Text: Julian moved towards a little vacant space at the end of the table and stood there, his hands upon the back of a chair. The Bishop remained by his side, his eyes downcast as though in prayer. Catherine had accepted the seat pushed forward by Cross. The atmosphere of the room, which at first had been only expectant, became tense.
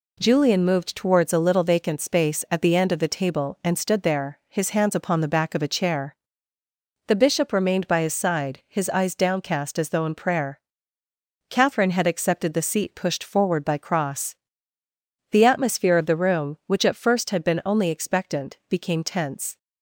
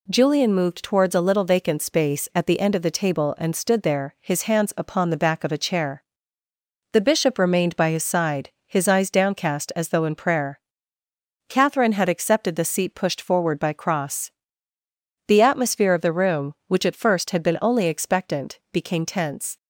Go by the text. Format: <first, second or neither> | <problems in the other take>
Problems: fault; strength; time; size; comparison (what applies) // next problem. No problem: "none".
neither | none